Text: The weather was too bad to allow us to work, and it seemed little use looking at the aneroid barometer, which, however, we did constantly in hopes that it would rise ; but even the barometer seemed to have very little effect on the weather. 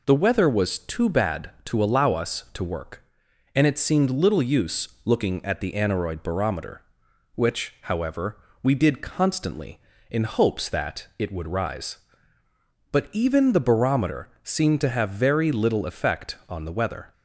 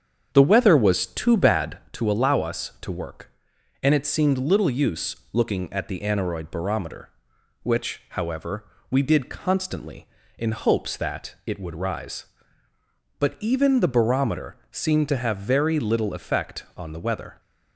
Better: first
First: pauses between "use" and "looking"; slight; at 4.8 s; 0.16 s long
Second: starts louder than the rest; strong; until 1.9 s; 7.5 dB // pauses between "use" and "looking"; slight; at 5.1 s; 0.16 s long

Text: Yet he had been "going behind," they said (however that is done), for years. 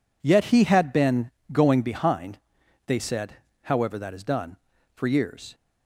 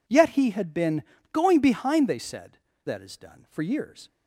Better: first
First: pauses between "been" and "going"; slight; at 1.3 s; 0.22 s long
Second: pauses between "been" and "going"; slight; at 1.0 s; 0.30 s long // skips "however"; at 2.7 s

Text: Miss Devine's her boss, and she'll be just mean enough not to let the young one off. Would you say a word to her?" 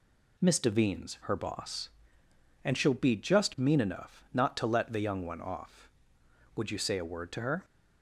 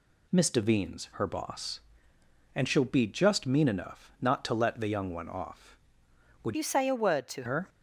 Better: first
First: none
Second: changes voice from "you" to "to"; from 6.5 to 7.4 s; 0.9 s long

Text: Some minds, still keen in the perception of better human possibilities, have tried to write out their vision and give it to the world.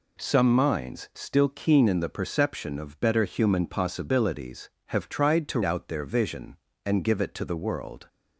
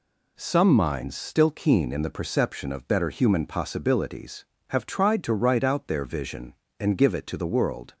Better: second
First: skips "write"; at 5.6 s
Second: none

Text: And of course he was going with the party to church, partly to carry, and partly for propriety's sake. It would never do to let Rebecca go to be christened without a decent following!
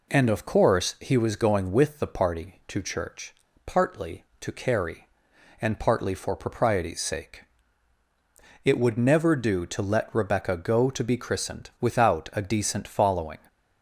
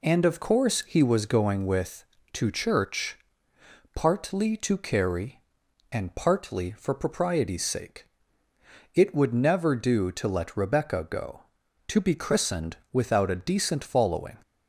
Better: first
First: none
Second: skips "the party"; at 2.1 s // pauses between "christened" and "without"; slight; at 12.7 s; 0.16 s long

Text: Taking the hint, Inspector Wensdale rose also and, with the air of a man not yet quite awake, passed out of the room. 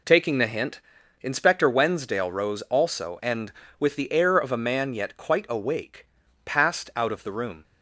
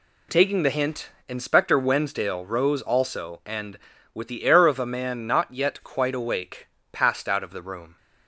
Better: second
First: skips "not"; at 4.9 s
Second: none

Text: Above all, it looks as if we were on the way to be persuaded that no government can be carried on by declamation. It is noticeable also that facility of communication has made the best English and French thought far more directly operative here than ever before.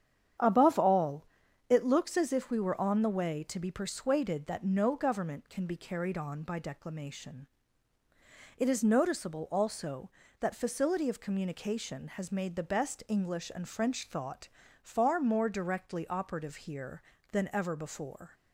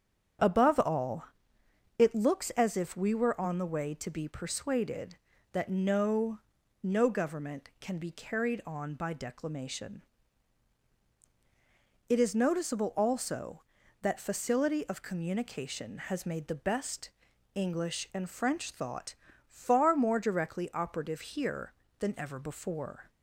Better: first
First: starts louder than the rest; strong; until 1.8 s; 9 dB // pauses between "thought" and "far"; slight; at 14.4 s; 0.36 s long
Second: starts louder than the rest; strong; until 2.1 s; 8.5 dB // says "no" twice; at 6.8 s // pauses between "best" and "English"; at 17.1 s; 0.44 s long // pauses between "thought" and "far"; slight; at 19.1 s; 0.32 s long

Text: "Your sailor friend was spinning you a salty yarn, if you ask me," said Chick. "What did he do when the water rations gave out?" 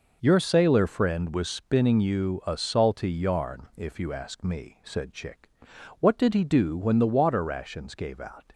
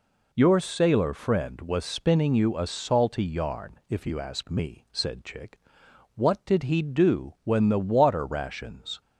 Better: first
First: none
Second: stops before "gave out"; at 9.0 s

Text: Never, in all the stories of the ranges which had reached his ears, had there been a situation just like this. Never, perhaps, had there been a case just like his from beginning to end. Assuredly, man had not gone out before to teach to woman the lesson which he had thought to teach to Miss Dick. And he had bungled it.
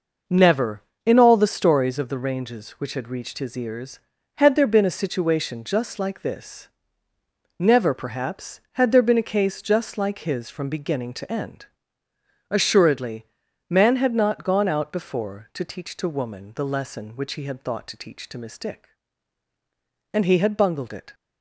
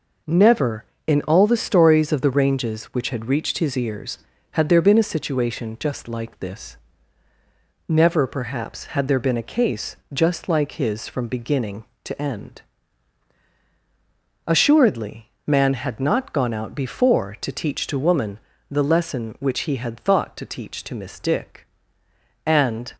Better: first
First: none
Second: pauses between "case" and "just"; slight; at 9.9 s; 0.16 s long // pauses between "woman" and "the"; slight; at 18.3 s; 0.32 s long // stops before "he had bungled it"; at 22.9 s

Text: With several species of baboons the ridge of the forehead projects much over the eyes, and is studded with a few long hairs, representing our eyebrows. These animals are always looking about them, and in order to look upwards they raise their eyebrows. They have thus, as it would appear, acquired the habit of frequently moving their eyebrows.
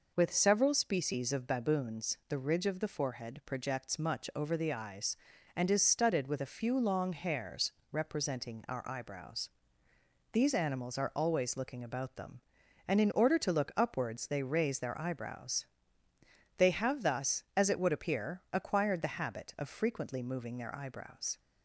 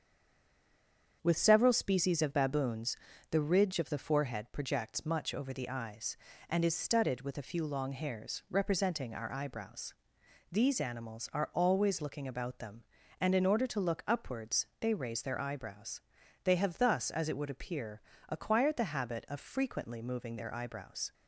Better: first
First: none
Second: stays silent before the first word; noticeable; until 1.2 s; 1.2 s long // starts louder than the rest; strong; until 2.2 s; 7.5 dB // pauses between "baboons" and "the"; slight; at 2.9 s; 0.36 s long

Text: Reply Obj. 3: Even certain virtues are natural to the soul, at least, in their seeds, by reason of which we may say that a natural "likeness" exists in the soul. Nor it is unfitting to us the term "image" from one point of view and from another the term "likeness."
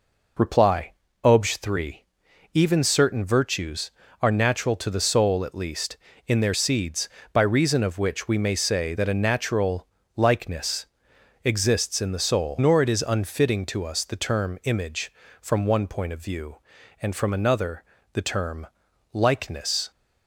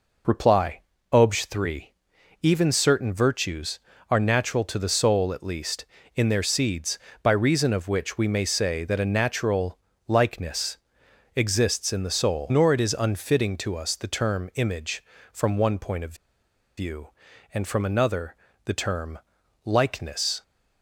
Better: first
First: pauses between "Reply" and "Obj"; slight; at 0.9 s; 0.32 s long // pauses between "natural" and "likeness"; slight; at 9.8 s; 0.30 s long // pauses between "likeness" and "exists"; noticeable; at 10.8 s; 0.58 s long // pauses between "another" and "the"; slight; at 17.8 s; 0.28 s long // pauses between "term" and "likeness"; noticeable; at 18.6 s; 0.46 s long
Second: pauses between "Reply" and "Obj"; slight; at 0.7 s; 0.32 s long // pauses between "natural" and "likeness"; slight; at 9.7 s; 0.30 s long // pauses between "likeness" and "exists"; noticeable; at 10.7 s; 0.58 s long // pauses between "of" and "view"; noticeable; at 16.1 s; 0.61 s long // pauses between "another" and "the"; slight; at 18.3 s; 0.28 s long // pauses between "term" and "likeness"; noticeable; at 19.1 s; 0.46 s long

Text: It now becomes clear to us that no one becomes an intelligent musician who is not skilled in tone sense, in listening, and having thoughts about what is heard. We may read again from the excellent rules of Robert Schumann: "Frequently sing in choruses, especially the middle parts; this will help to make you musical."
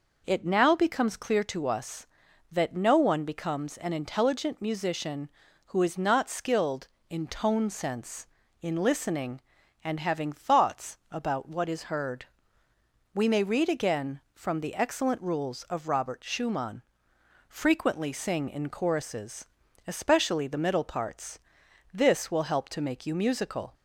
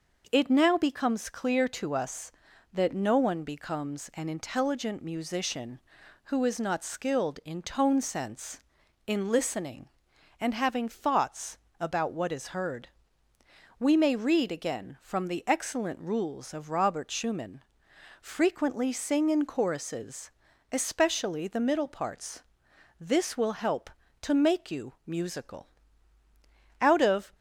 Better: first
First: none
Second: pauses between "thoughts" and "about"; slight; at 11.5 s; 0.22 s long // goes on to say "Out of"; from 26.8 s on; 0.50 s long

